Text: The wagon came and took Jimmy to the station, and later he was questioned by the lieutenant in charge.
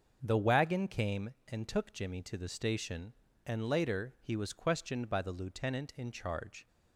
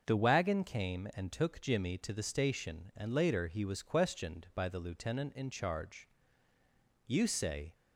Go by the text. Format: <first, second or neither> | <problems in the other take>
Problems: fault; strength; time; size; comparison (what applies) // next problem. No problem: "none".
first | starts louder than the rest; noticeable; until 1.0 s; 6 dB; also in the first // goes on to say "You say"; noticeable; from 7.0 s on; 0.68 s long